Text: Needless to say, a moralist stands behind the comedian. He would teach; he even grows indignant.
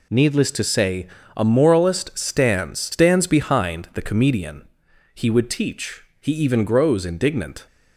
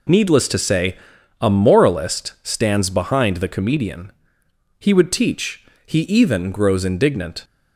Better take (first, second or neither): second